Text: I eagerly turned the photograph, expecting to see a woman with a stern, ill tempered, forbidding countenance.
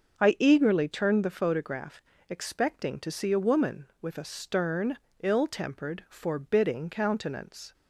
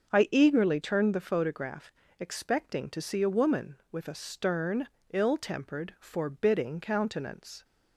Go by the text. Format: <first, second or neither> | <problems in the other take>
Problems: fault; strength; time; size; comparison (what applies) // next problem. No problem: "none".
neither | starts louder than the rest; the same in both